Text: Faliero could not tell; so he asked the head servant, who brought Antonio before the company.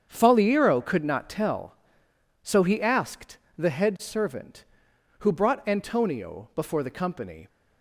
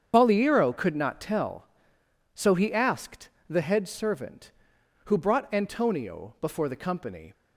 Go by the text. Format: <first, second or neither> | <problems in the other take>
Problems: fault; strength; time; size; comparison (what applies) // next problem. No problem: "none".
first | loses the start of "Faliero"; at 0.1 s; 120 ms // starts louder than the rest; strong; until 1.1 s; 7.5 dB; strong in the first // pauses between "asked" and "the"; slight; at 3.2 s; 0.20 s long; slight in the first